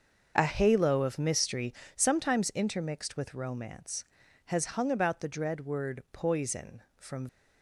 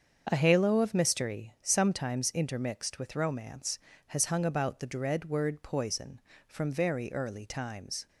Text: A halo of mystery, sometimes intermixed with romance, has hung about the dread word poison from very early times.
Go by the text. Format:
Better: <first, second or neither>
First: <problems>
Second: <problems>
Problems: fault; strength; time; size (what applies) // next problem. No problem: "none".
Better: second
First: starts louder than the rest; noticeable; until 1.3 s; 6 dB // stops before "very early times"; at 7.2 s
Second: starts louder than the rest; until 1.3 s; 7 dB